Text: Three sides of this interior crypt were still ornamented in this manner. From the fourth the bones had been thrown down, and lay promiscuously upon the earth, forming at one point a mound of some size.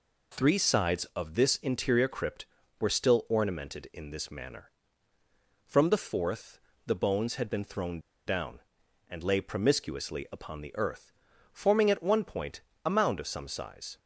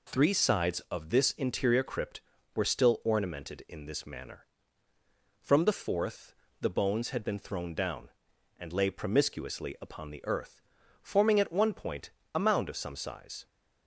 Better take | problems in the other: second | pauses between "fourth" and "the"; slight; at 6.5 s; 0.28 s long; slight in the second // pauses between "thrown" and "down"; slight; at 8.0 s; 0.26 s long // pauses between "point" and "a"; slight; at 12.6 s; 0.22 s long; slight in the second

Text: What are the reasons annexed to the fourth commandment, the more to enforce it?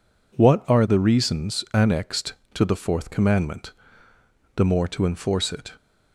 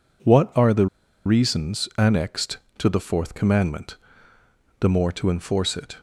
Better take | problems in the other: first | pauses between "the" and "reasons"; at 0.8 s; 0.39 s long

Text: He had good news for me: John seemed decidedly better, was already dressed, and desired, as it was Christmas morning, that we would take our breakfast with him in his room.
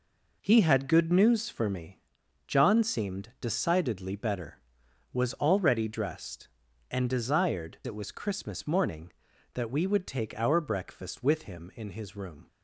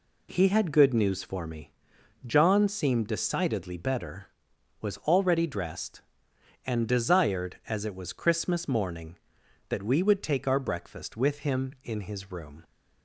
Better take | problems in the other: second | skips "as"; at 7.8 s

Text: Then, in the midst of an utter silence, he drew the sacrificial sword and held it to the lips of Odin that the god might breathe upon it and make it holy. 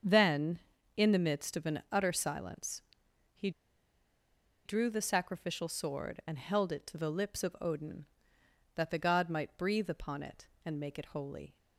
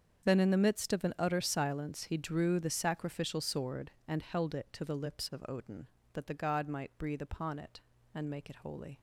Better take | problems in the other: second | starts louder than the rest; strong; until 1.4 s; 7.5 dB; strong in the second // pauses between "he" and "drew"; at 3.4 s; 1.1 s long

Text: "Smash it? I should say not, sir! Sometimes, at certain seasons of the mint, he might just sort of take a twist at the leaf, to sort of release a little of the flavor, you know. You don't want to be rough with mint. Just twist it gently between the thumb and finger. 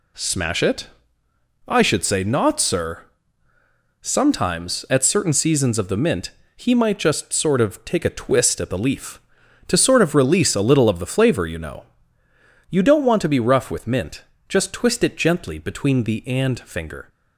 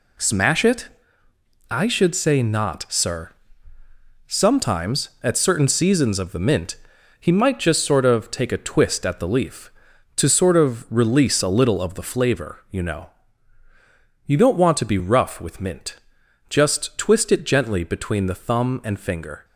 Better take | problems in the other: second | skips "thumb"; at 16.2 s

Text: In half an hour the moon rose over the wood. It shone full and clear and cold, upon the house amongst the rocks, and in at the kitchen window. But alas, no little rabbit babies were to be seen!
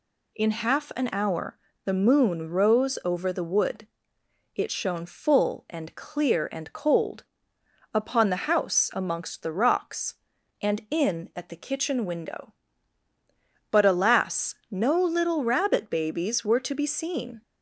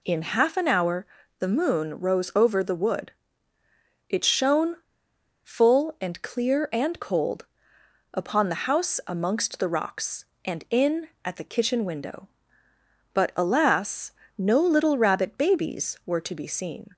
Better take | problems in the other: first | pauses between "hour" and "the"; slight; at 1.0 s; 0.32 s long; slight in the first // pauses between "shone" and "full"; noticeable; at 4.7 s; 0.68 s long

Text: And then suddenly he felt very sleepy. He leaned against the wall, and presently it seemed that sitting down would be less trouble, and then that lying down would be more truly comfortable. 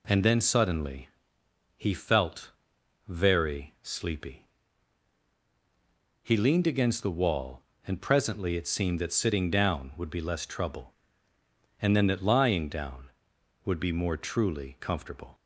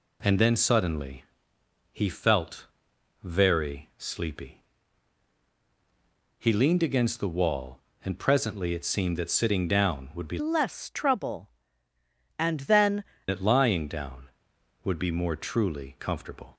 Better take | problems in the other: first | pauses between "suddenly" and "he"; noticeable; at 1.2 s; 0.68 s long; noticeable in the first // pauses between "felt" and "very"; noticeable; at 2.6 s; 0.58 s long; noticeable in the first // changes voice from "less" to "then"; from 10.3 to 13.0 s; 2.7 s long

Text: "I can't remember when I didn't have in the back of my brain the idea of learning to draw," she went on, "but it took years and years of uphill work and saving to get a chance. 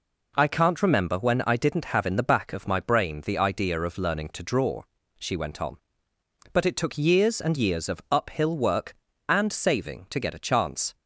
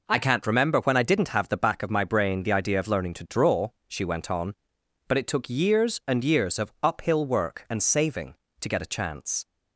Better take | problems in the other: first | skips "in"; at 1.4 s

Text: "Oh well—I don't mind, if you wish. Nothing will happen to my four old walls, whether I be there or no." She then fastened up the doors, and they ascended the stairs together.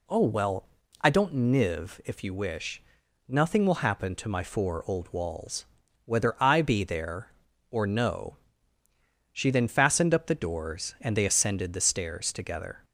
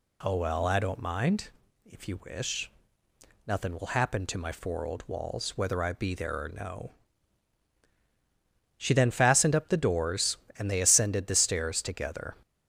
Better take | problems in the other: second | says "niv" for "mind"; at 1.3 s

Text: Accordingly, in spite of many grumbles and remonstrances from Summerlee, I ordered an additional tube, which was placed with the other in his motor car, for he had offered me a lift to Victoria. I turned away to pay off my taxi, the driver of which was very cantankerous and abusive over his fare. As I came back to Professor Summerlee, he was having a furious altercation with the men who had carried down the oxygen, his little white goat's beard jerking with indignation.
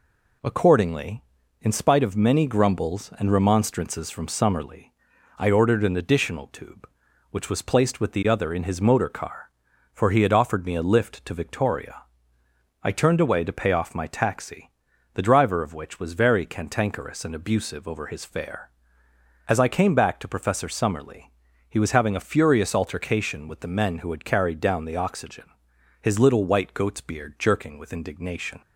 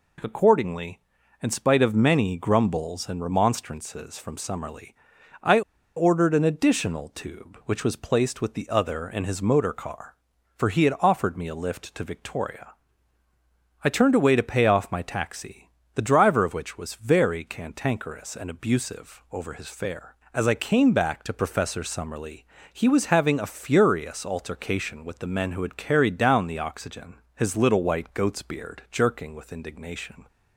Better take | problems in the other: first | pauses between "I" and "ordered"; slight; at 5.6 s; 0.35 s long

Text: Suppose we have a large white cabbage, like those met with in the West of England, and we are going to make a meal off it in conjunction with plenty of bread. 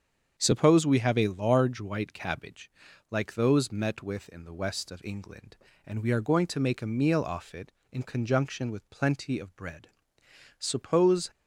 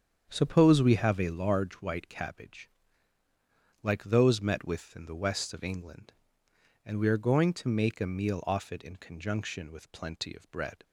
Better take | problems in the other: second | starts louder than the rest; strong; until 1.3 s; 7.5 dB; strong in the second // goes on to say "Suppose"; noticeable; from 10.5 s on; 0.72 s long

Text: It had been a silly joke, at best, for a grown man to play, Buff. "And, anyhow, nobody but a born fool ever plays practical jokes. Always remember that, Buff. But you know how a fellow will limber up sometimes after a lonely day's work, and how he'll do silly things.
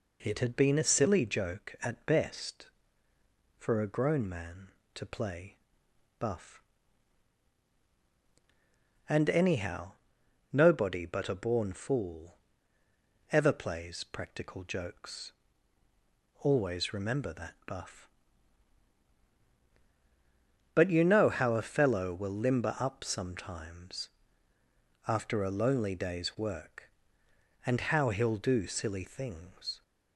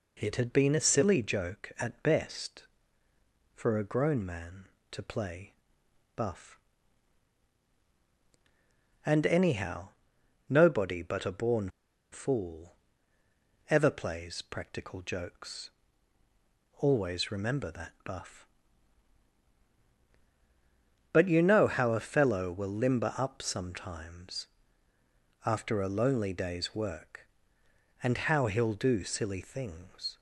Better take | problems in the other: first | pauses between "born" and "fool"; at 11.6 s; 0.42 s long // pauses between "fool" and "ever"; noticeable; at 12.7 s; 0.94 s long; noticeable in the first // pauses between "sometimes" and "after"; noticeable; at 24.4 s; 0.98 s long; noticeable in the first

